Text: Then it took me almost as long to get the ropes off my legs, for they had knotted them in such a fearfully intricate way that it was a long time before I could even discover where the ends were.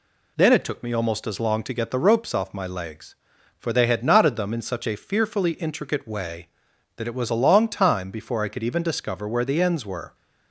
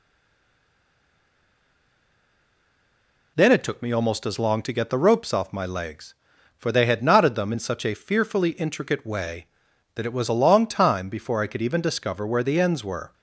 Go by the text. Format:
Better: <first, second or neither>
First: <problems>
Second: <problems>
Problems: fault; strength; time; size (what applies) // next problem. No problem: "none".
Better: first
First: none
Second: stays silent before the first word; strong; until 3.3 s; 3.3 s long